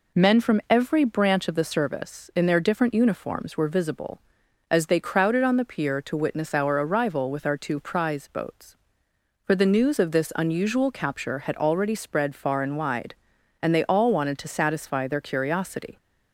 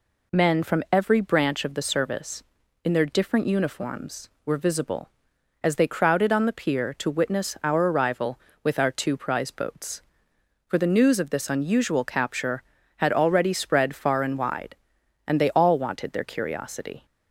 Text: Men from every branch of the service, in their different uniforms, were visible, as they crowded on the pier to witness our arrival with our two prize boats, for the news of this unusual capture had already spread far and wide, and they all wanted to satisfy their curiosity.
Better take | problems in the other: first | skips "to satisfy"; at 16.1 s

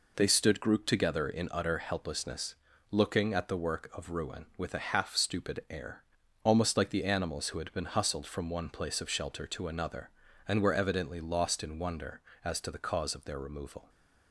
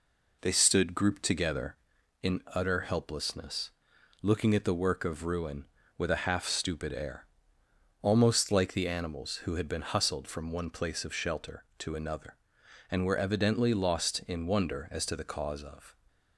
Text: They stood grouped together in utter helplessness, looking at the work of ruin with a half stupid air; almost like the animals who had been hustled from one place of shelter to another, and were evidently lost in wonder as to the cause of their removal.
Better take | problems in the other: first | stops before "their removal"; at 16.0 s

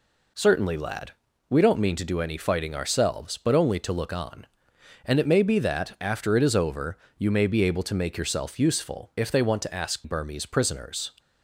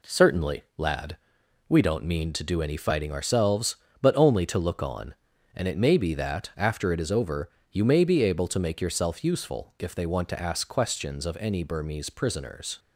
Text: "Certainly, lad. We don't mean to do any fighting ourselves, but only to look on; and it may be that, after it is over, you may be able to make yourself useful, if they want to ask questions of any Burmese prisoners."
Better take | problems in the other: second | skips "questions of any"; at 10.0 s

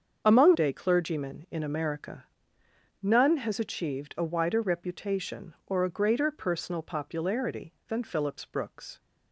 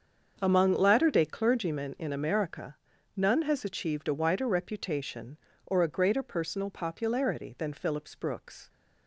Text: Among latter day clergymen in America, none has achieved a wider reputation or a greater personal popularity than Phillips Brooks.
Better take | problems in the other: second | starts louder than the rest; until 1.2 s; 7 dB; also in the second // skips "latter"; at 0.5 s

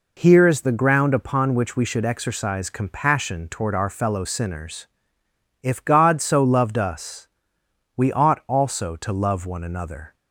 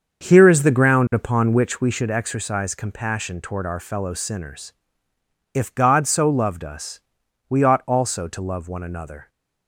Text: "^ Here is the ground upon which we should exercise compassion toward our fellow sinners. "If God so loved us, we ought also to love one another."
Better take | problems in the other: first | starts louder than the rest; until 1.9 s; 6.5 dB

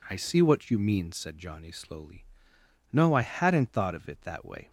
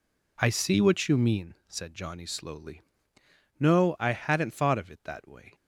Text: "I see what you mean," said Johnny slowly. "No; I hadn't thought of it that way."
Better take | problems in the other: neither | none

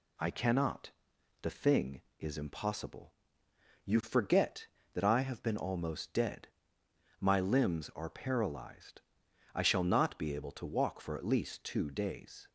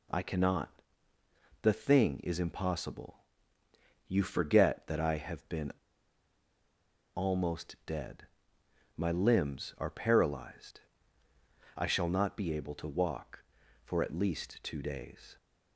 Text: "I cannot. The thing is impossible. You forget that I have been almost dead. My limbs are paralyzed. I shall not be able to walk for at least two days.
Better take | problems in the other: first | pauses between "been" and "almost"; strong; at 5.7 s; 1.4 s long

